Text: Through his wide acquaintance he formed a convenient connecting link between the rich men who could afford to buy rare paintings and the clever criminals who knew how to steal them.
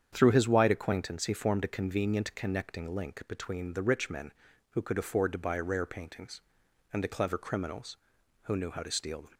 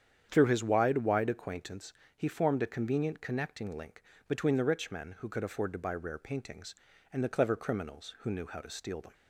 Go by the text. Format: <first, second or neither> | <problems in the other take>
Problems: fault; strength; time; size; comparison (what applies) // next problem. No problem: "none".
first | starts louder than the rest; strong; until 1.3 s; 8.5 dB; strong in the first // says "wide" twice; at 0.9 s // pauses between "acquaintance" and "he"; slight; at 1.9 s; 0.22 s long // pauses between "link" and "between"; slight; at 4.0 s; 0.24 s long